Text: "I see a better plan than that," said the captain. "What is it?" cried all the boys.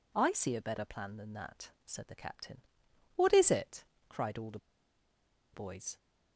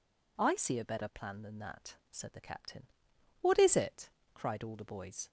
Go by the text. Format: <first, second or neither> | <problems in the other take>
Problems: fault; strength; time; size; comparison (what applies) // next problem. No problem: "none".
second | pauses between "the" and "boys"; noticeable; at 4.5 s; 0.96 s long